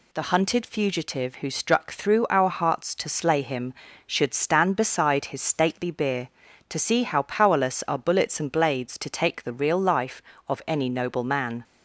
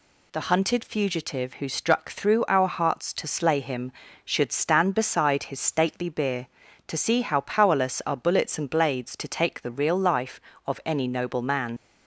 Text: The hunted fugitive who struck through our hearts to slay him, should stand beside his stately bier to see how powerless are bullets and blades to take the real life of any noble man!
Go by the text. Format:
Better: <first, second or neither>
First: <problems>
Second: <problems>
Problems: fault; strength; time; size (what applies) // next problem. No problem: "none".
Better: first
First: none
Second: leaves "man" unfinished; at 11.7 s; 50 ms